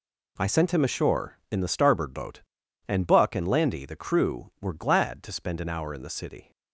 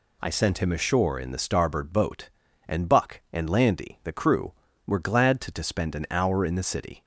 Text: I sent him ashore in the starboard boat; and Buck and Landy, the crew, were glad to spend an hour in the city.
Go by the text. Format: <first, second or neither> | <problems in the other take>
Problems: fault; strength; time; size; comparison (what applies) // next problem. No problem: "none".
first | says "to" twice; at 5.5 s